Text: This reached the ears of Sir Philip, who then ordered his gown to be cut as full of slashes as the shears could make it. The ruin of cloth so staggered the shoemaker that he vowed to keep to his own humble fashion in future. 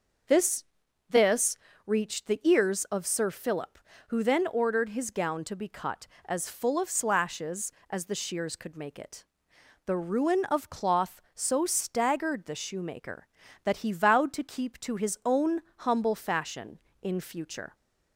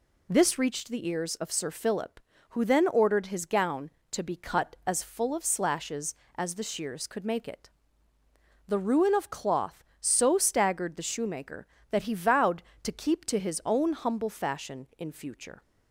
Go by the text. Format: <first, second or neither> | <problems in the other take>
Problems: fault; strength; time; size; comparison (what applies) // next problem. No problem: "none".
second | starts louder than the rest; noticeable; until 2.0 s; 6 dB // says "This" twice; at 1.0 s // pauses between "own" and "humble"; slight; at 15.6 s; 0.18 s long